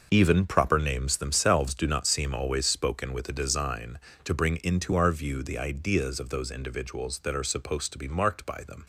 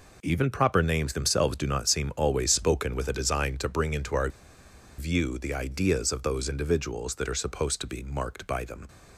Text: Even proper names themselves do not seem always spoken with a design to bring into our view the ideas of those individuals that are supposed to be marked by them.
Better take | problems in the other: first | pauses between "our" and "view"; noticeable; at 4.2 s; 0.70 s long

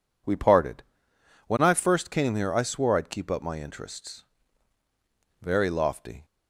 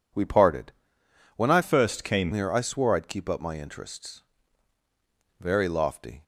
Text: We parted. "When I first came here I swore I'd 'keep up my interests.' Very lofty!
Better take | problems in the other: first | changes voice from "first" to "came"; from 1.6 to 2.3 s; 0.7 s long

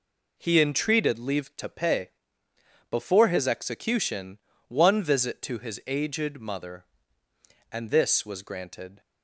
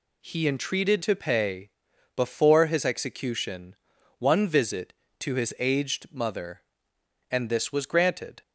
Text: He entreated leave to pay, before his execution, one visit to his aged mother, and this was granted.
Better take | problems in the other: first | skips "leave"; at 1.0 s

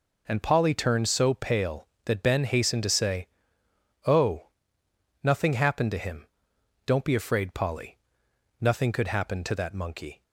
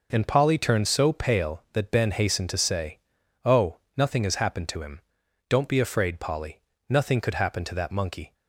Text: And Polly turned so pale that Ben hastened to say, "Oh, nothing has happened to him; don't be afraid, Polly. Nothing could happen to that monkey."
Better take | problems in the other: second | skips "has"; at 5.5 s

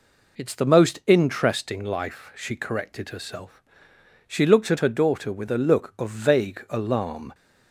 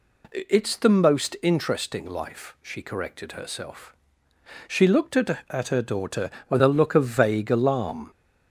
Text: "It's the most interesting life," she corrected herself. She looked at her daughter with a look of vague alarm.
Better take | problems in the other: first | says "at" twice; at 5.5 s

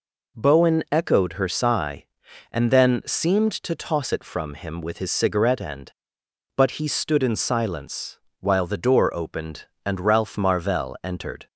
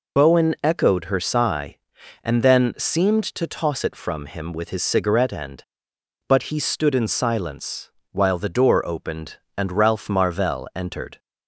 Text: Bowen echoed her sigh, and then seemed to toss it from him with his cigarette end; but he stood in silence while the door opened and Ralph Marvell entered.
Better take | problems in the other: first | loses the start of "Bowen"; at 0.1 s; 95 ms // pauses between "silence" and "while"; slight; at 7.9 s; 0.22 s long; slight in the first

